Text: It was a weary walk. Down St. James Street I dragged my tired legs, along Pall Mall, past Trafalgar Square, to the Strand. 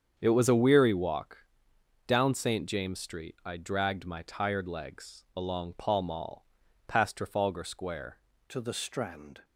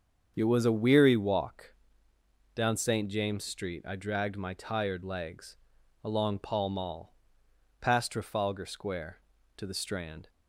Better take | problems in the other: second | starts louder than the rest; strong; until 1.1 s; 7.5 dB; also in the second // changes voice at "to"; from 8.4 s on; 1.0 s long

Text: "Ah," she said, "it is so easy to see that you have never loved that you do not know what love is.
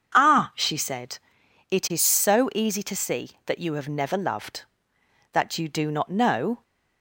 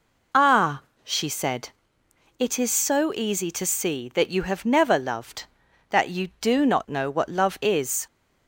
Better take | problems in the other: second | stops before "what love is"; at 6.6 s

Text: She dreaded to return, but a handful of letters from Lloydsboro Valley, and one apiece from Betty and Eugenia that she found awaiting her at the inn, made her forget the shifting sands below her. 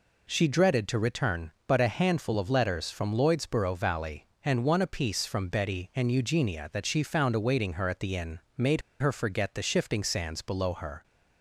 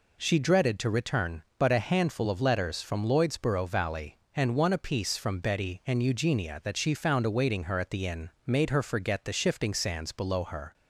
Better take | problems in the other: second | pauses between "made" and "her"; slight; at 8.8 s; 0.19 s long

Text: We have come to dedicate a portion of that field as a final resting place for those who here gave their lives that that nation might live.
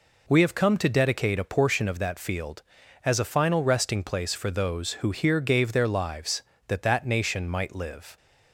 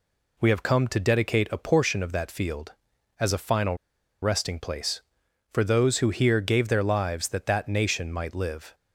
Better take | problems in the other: first | pauses between "final" and "resting"; noticeable; at 3.7 s; 0.47 s long

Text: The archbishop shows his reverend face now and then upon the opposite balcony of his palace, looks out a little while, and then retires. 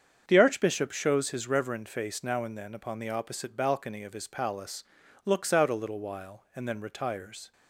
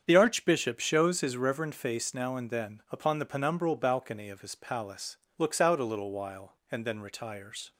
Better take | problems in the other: first | starts louder than the rest; strong; until 1.0 s; 7.5 dB; strong in the first // says "penumbral" for "opposite"; at 3.2 s

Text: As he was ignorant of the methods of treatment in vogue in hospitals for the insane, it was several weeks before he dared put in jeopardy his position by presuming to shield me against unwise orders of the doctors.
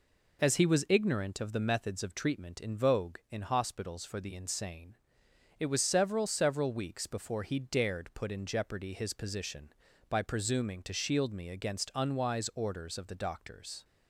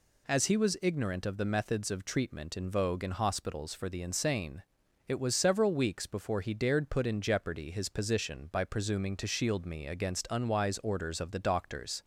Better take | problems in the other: second | says "several" twice; at 6.2 s

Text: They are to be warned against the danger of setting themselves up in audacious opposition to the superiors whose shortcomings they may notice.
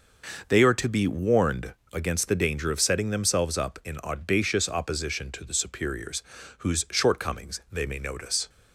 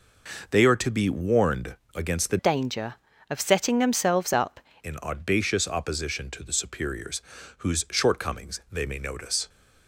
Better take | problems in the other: first | pauses between "warned" and "against"; slight; at 1.7 s; 0.18 s long; slight in the first // changes voice from "danger" to "up"; from 2.3 to 4.5 s; 2.2 s long // pauses between "superiors" and "whose"; at 7.2 s; 0.38 s long; also in the first

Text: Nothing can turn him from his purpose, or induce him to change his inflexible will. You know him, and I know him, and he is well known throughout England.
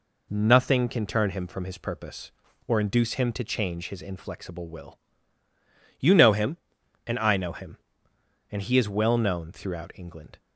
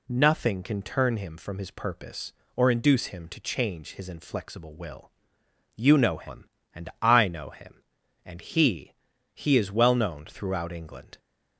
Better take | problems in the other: first | says "he" twice; at 9.3 s

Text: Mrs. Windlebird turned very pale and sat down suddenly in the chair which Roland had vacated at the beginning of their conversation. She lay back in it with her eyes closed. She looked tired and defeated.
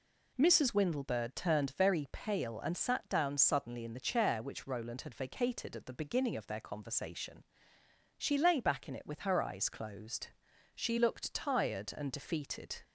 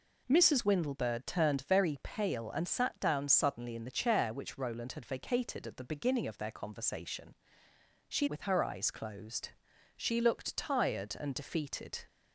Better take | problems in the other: first | skips "lay back in it"; at 8.2 s

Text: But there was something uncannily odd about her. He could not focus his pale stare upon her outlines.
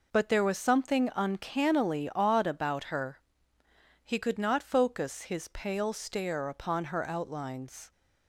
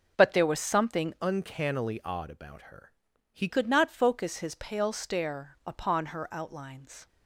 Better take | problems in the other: first | changes voice from "uncannily" to "He"; from 1.2 to 3.4 s; 2.2 s long

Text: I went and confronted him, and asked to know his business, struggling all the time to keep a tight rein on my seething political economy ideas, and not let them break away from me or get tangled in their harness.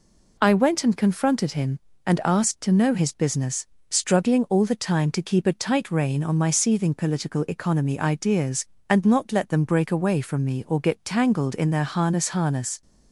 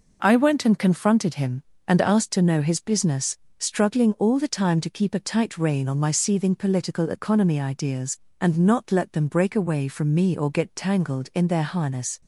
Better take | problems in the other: second | says "harness" twice; at 12.2 s

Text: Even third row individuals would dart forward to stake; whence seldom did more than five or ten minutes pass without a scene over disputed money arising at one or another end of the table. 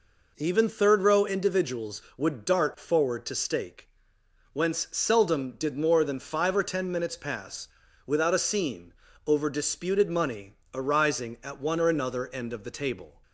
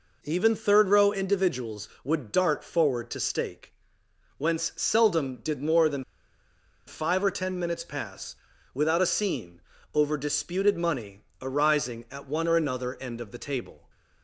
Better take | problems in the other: first | pauses between "than" and "five"; noticeable; at 6.0 s; 0.83 s long // pauses between "pass" and "without"; at 8.3 s; 0.38 s long; also in the first // pauses between "scene" and "over"; slight; at 9.5 s; 0.34 s long; slight in the first // pauses between "money" and "arising"; slight; at 11.1 s; 0.22 s long; slight in the first

